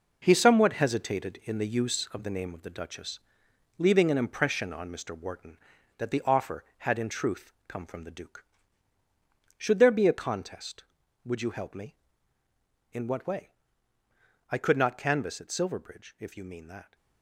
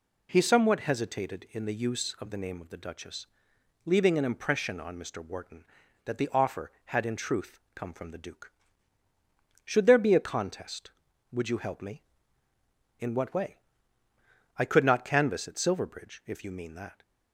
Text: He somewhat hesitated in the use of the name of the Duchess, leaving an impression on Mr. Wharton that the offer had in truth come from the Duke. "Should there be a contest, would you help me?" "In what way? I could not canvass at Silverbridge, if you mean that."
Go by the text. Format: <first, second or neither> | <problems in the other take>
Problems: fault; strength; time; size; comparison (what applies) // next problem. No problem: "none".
second | gets quieter; strong; throughout; 9 dB // pauses between "truth" and "come"; slight; at 7.5 s; 0.16 s long; slight in the second